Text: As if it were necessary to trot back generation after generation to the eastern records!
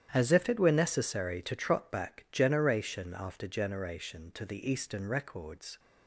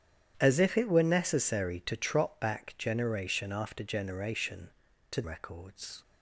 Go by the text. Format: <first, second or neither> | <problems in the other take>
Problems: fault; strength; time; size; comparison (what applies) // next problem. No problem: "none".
first | starts louder than the rest; strong; until 1.3 s; 10 dB; strong in the first // skips "the eastern"; at 5.2 s